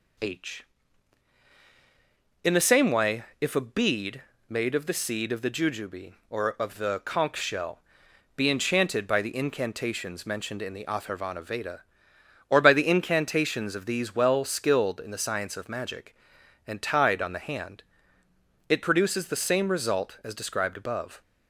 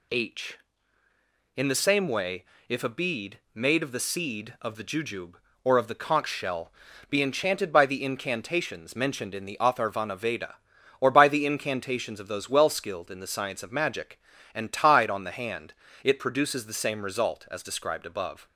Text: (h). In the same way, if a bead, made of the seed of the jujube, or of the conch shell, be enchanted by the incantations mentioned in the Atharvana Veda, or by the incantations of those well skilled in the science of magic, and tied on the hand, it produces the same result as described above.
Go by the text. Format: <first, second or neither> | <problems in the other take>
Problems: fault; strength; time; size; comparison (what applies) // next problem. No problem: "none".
second | says "these" for "those"; at 13.8 s